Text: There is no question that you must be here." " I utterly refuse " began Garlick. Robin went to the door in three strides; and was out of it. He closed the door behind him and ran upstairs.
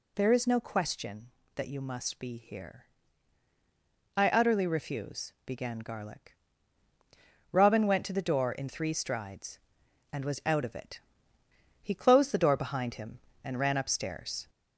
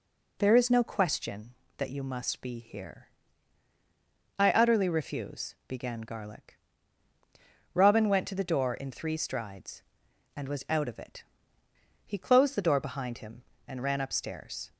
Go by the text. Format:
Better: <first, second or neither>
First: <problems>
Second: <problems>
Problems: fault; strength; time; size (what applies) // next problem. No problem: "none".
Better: second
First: gets louder; strong; throughout; 7 dB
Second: none